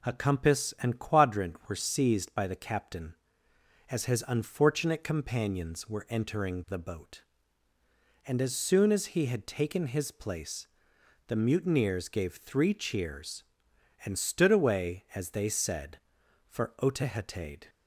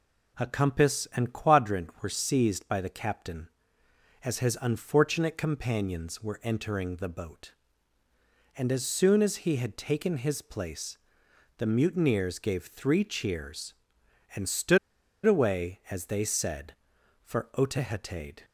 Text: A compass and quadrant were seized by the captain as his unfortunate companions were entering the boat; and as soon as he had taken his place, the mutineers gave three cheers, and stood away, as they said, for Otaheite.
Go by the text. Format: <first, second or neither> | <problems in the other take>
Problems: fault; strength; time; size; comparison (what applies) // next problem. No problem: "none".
first | pauses between "stood" and "away"; noticeable; at 14.7 s; 0.48 s long